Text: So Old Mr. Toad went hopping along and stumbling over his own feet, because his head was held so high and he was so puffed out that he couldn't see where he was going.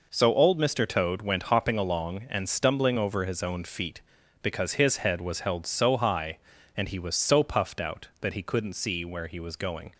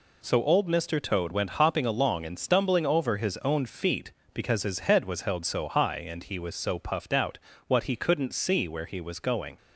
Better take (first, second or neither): first